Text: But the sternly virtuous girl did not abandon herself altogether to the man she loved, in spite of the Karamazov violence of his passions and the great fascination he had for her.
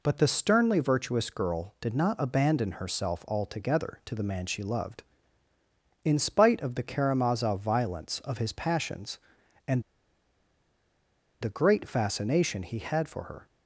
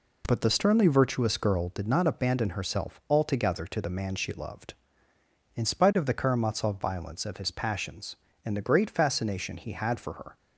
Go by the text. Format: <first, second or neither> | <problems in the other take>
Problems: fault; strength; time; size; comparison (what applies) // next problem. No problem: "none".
second | pauses between "and" and "the"; strong; at 9.8 s; 1.5 s long